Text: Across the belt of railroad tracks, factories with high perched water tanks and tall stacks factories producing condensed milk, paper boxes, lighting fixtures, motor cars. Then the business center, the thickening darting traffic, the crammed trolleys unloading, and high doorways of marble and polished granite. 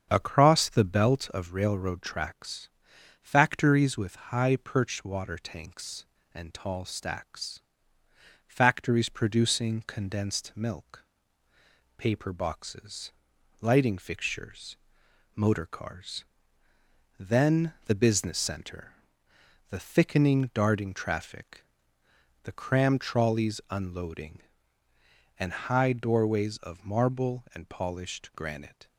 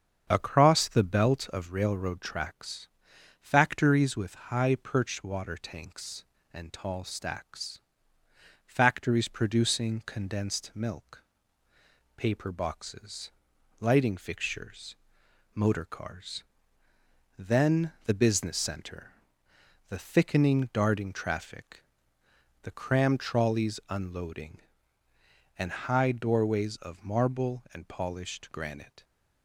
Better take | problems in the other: neither | starts louder than the rest; strong; the same in both // pauses between "stacks" and "factories"; noticeable; the same in both

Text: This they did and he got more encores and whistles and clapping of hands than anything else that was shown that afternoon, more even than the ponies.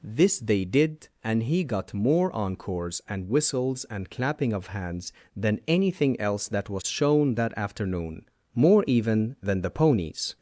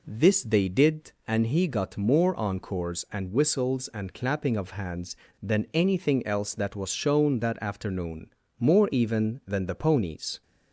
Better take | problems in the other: second | gets louder; slight; throughout; 3 dB

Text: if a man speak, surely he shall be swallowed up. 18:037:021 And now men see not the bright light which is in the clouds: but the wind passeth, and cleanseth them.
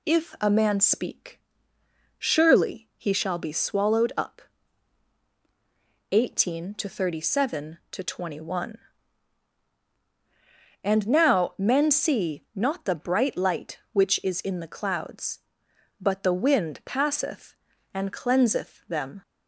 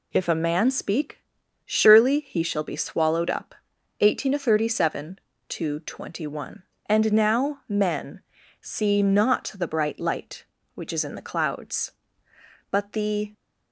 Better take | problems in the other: first | pauses between "men" and "see"; at 8.2 s; 0.40 s long // stops before "wind passeth and cleanseth them"; at 13.3 s

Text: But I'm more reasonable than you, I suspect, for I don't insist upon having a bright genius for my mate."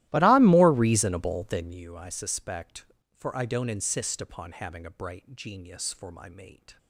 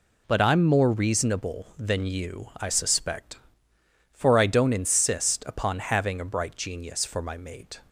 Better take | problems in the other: second | starts louder than the rest; strong; until 1.9 s; 15.5 dB

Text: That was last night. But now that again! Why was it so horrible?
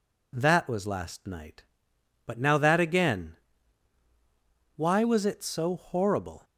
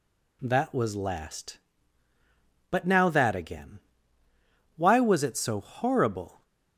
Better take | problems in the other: first | skips "night"; at 2.1 s

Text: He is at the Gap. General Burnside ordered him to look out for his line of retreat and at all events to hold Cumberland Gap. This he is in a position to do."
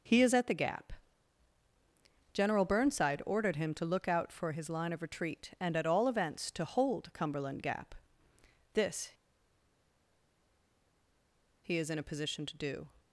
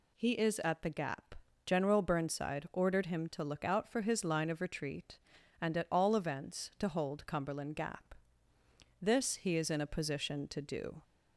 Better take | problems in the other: second | pauses between "This" and "he"; strong; at 9.1 s; 2.5 s long

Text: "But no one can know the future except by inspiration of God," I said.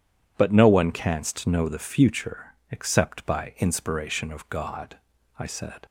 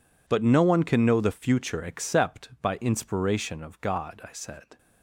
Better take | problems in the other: second | says "canst" for "can"; at 0.9 s // pauses between "future" and "except"; slight; at 2.5 s; 0.16 s long

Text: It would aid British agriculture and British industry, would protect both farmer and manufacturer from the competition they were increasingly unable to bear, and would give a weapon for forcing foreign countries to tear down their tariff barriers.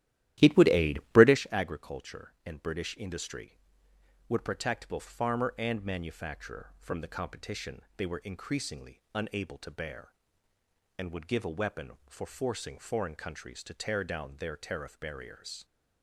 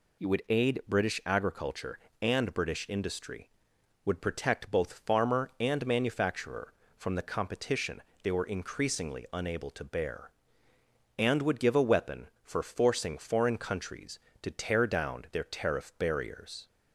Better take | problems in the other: second | starts louder than the rest; strong; until 1.4 s; 13.5 dB // pauses between "competition" and "they"; slight; at 7.8 s; 0.16 s long; slight in the second

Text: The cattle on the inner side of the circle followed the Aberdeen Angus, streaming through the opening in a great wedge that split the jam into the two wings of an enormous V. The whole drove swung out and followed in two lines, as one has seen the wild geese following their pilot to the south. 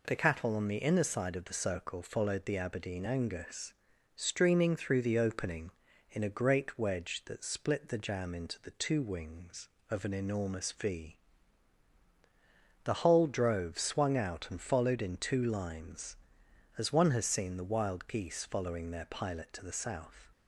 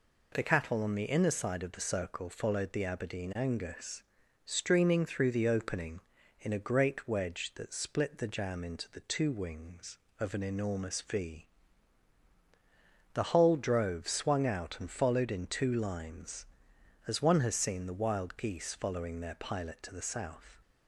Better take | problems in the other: neither | none

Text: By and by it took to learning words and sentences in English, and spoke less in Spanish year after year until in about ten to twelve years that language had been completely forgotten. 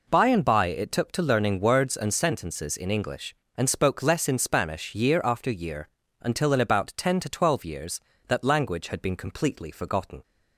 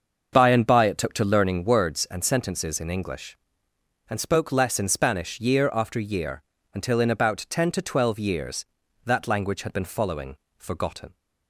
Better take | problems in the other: first | starts louder than the rest; until 1.3 s; 6.5 dB // pauses between "year" and "until"; slight; at 6.4 s; 0.32 s long; slight in the first // says "following" for "completely"; at 9.8 s

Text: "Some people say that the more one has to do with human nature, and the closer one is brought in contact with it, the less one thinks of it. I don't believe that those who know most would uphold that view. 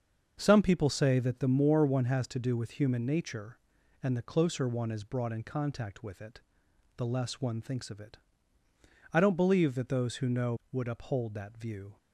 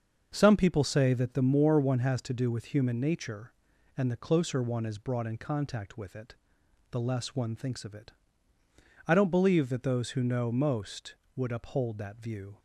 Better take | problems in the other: second | starts louder than the rest; until 1.4 s; 6.5 dB; also in the second // skips "most"; at 10.6 s

